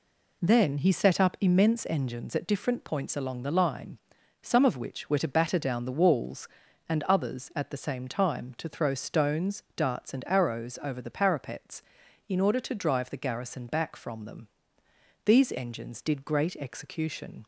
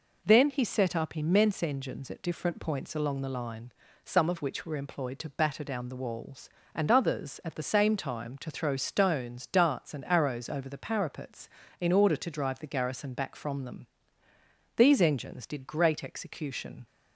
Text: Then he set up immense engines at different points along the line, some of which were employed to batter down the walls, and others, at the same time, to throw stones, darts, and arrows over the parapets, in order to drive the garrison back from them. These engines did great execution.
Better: second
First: skips "employed"; at 5.1 s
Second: none

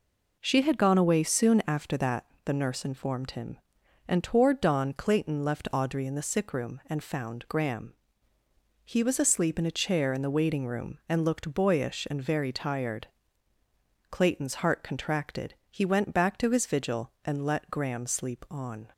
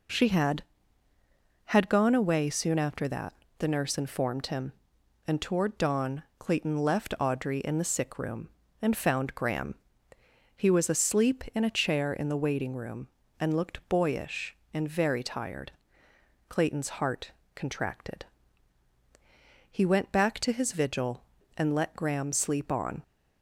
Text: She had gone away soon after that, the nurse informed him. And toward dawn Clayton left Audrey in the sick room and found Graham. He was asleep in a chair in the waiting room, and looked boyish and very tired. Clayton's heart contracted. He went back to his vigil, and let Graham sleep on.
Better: first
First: none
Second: says "had" twice; at 1.6 s // pauses between "dawn" and "Clayton"; slight; at 6.2 s; 0.18 s long // pauses between "heart" and "contracted"; slight; at 17.3 s; 0.24 s long

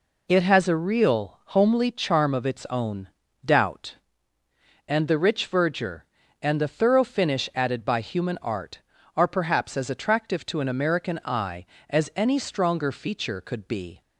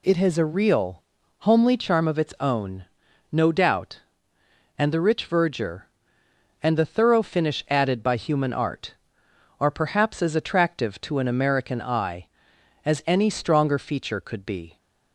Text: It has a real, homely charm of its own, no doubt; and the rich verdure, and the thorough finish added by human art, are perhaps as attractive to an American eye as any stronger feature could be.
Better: second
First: skips "no"; at 3.2 s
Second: none

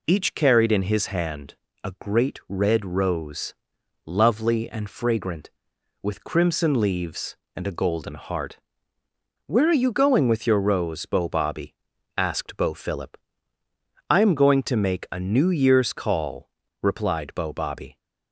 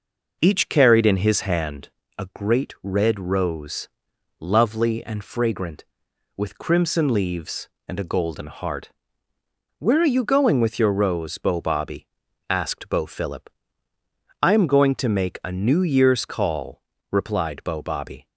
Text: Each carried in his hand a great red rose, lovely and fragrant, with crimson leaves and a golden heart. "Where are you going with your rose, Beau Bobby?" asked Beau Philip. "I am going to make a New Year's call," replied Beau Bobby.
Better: first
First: pauses between "hand" and "a"; slight; at 1.5 s; 0.30 s long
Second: starts louder than the rest; noticeable; until 2.0 s; 5.5 dB // pauses between "hand" and "a"; slight; at 1.8 s; 0.30 s long

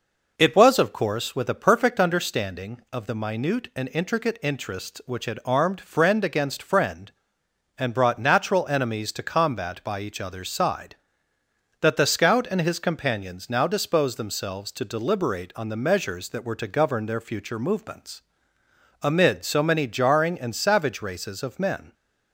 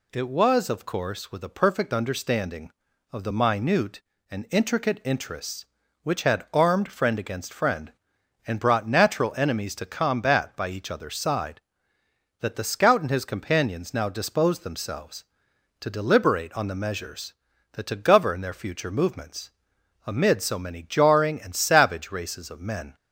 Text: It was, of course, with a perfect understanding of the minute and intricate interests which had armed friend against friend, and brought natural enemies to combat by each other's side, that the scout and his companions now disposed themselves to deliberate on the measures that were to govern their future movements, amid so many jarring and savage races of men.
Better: first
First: none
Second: skips "were"; at 17.8 s

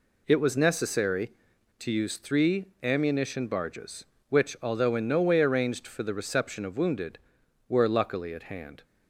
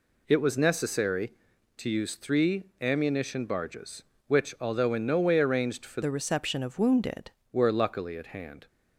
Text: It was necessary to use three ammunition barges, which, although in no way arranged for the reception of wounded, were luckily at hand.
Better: first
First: pauses between "three" and "ammunition"; slight; at 2.6 s; 0.16 s long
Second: pauses between "three" and "ammunition"; slight; at 2.6 s; 0.16 s long // changes voice from "the" to "wounded"; from 6.0 to 7.3 s; 1.3 s long

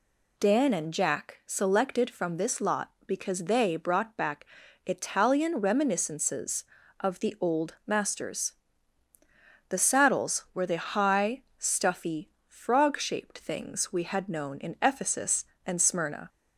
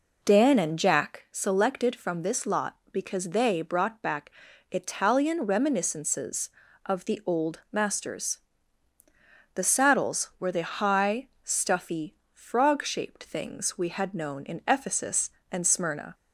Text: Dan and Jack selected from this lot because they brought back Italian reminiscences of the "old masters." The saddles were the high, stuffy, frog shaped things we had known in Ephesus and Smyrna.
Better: first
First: pauses between "back" and "Italian"; at 4.4 s; 0.40 s long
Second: starts louder than the rest; noticeable; until 1.2 s; 4.5 dB // pauses between "back" and "Italian"; at 4.2 s; 0.40 s long

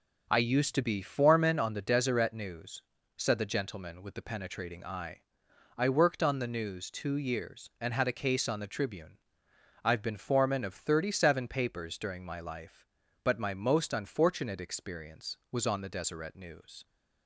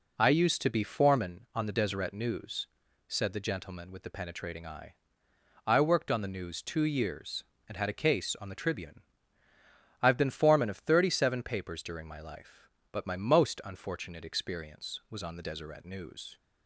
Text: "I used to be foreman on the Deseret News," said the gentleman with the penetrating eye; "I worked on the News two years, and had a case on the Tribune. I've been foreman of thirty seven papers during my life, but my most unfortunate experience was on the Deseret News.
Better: neither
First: none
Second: none

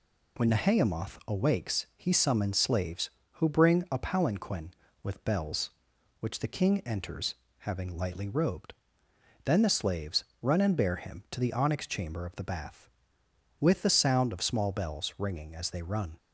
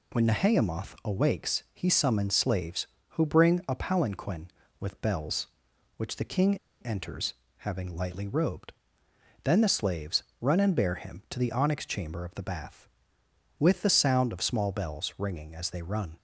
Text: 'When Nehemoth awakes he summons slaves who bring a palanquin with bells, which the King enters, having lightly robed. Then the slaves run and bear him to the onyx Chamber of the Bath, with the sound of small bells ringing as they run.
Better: first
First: pauses between "slaves" and "run"; slight; at 10.2 s; 0.18 s long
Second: pauses between "King" and "enters"; slight; at 6.5 s; 0.23 s long // pauses between "slaves" and "run"; slight; at 10.2 s; 0.18 s long

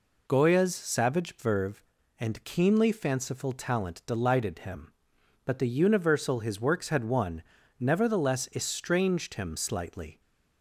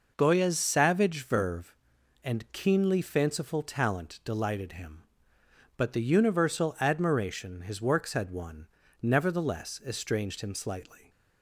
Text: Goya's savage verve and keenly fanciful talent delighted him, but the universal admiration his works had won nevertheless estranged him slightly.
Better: second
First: skips "admiration"; at 6.3 s // pauses between "won" and "nevertheless"; at 7.4 s; 0.38 s long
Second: pauses between "won" and "nevertheless"; slight; at 8.6 s; 0.34 s long

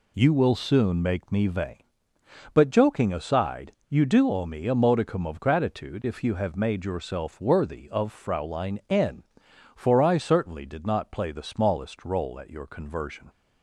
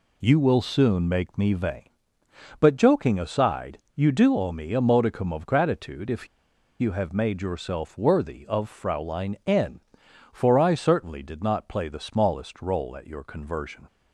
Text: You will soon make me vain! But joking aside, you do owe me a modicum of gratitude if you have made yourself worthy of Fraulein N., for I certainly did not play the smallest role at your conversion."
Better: first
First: none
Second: pauses between "if" and "you"; noticeable; at 6.2 s; 0.52 s long

